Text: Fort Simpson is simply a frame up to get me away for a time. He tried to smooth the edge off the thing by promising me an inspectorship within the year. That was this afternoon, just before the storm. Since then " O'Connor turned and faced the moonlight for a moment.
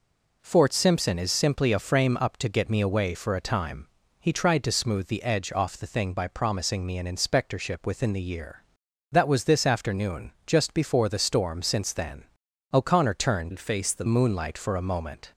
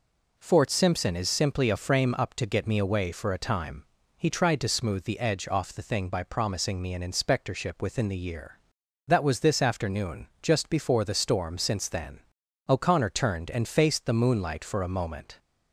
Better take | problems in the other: second | changes voice from "and" to "the"; from 13.5 to 14.0 s; 0.5 s long

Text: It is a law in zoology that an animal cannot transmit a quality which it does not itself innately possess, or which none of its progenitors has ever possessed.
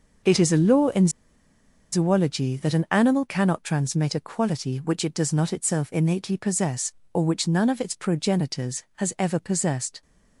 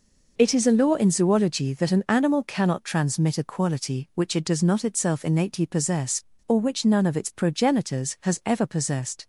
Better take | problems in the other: second | pauses between "in" and "zoology"; noticeable; at 1.0 s; 0.83 s long

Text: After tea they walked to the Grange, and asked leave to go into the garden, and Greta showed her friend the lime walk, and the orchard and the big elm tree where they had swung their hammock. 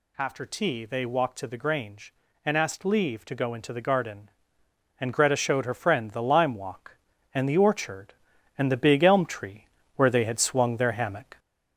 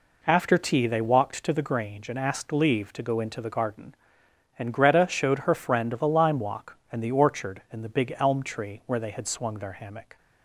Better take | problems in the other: second | gets louder; throughout; 3.5 dB // pauses between "tree" and "where"; slight; at 9.6 s; 0.30 s long

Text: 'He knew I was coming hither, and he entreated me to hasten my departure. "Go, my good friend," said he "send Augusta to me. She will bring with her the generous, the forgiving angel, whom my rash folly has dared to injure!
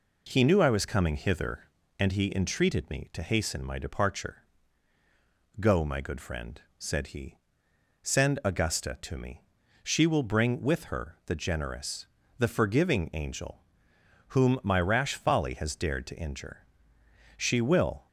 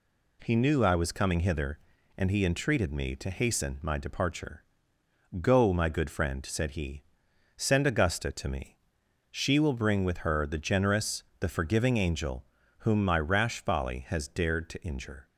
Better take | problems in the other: second | pauses between "he" and "send"; noticeable; at 7.3 s; 0.66 s long; noticeable in the second // goes on to say "She will"; noticeable; from 17.3 s on; 0.70 s long

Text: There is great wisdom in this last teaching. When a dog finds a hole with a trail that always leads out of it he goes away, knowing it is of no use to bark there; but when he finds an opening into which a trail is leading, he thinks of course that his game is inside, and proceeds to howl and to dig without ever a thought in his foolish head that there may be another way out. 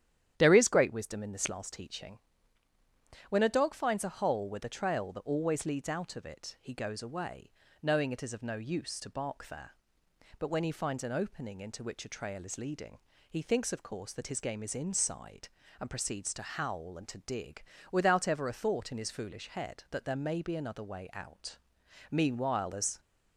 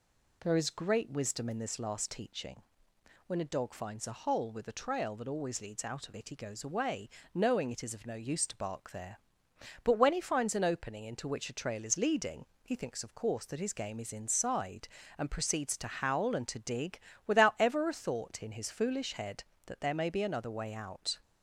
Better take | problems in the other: second | starts louder than the rest; strong; until 1.3 s; 10.5 dB // pauses between "dig" and "without"; slight; at 17.6 s; 0.26 s long; slight in the second // goes on to say "Meanwhile as"; noticeable; from 22.1 s on; 0.88 s long

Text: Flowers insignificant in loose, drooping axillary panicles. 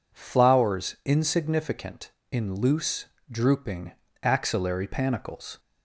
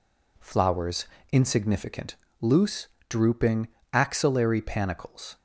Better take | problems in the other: first | pauses between "Flowers" and "insignificant"; slight; at 1.0 s; 0.25 s long // skips "in"; at 2.2 s // pauses between "drooping" and "axillary"; slight; at 3.6 s; 0.24 s long; slight in the first

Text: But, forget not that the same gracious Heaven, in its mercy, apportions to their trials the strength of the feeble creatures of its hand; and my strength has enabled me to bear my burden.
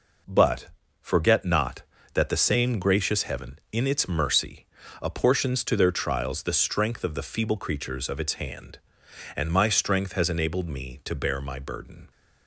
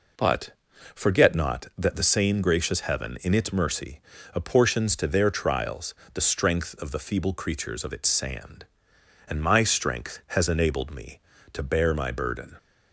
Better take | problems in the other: first | pauses between "trials" and "the"; slight; at 5.9 s; 0.20 s long // says "sand" for "hand"; at 8.0 s

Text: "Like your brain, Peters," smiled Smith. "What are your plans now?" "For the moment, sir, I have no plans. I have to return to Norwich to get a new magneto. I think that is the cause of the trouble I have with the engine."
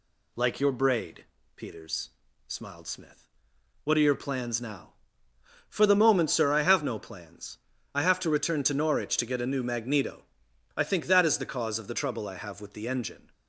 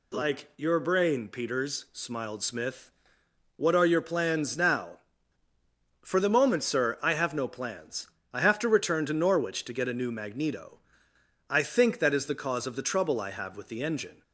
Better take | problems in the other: second | says "braid" for "brain"; at 0.7 s

